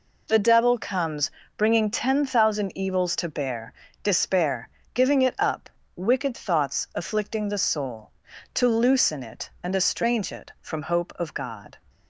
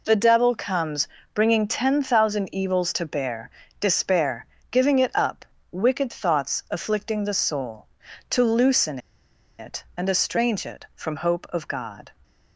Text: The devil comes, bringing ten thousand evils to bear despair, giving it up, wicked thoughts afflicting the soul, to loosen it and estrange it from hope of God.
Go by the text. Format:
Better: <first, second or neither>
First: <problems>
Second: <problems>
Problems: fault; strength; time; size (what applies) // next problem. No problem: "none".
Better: first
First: pauses between "bear" and "despair"; slight; at 3.7 s; 0.32 s long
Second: pauses between "bear" and "despair"; slight; at 3.4 s; 0.32 s long // pauses between "loosen" and "it"; noticeable; at 8.9 s; 0.61 s long